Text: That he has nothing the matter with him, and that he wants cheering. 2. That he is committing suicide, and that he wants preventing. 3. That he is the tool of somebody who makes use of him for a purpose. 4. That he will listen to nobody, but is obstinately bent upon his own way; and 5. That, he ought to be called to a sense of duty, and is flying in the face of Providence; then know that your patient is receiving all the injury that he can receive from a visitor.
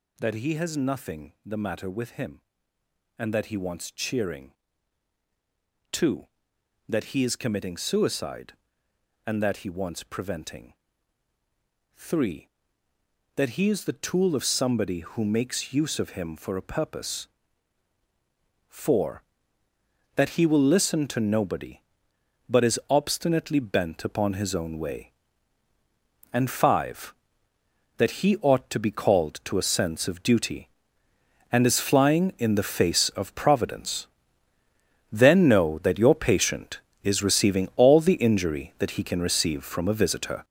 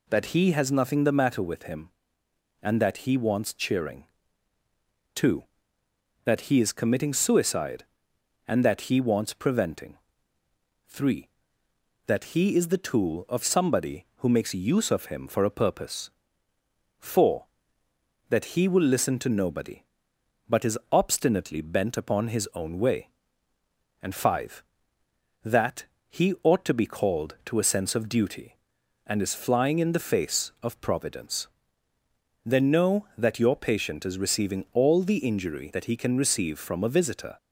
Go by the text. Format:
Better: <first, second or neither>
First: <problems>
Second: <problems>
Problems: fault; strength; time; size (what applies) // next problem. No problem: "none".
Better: second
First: gets louder; strong; throughout; 8.5 dB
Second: none